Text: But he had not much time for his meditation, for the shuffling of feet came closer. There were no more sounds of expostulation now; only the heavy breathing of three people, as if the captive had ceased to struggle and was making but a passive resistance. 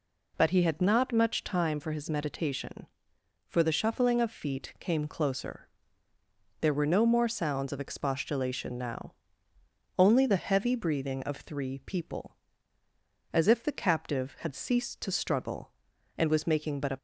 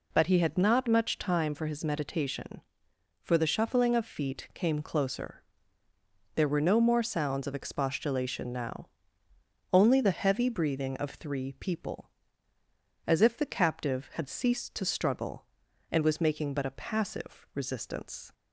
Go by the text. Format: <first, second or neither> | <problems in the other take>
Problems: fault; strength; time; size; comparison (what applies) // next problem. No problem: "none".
second | stops before "passive resistance"; at 16.9 s